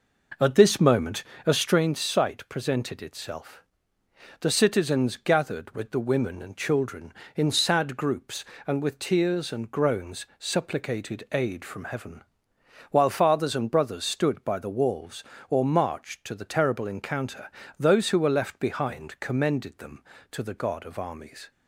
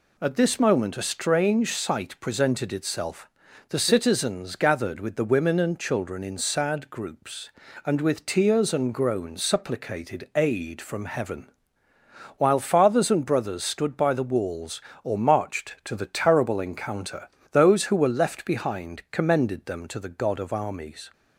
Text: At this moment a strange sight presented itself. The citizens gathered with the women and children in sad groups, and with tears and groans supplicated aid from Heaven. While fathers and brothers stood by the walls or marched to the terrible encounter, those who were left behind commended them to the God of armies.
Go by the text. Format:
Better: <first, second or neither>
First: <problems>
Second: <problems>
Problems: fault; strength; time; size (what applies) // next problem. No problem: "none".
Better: second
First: starts louder than the rest; noticeable; until 1.8 s; 5 dB // pauses between "moment" and "a"; slight; at 1.2 s; 0.22 s long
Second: none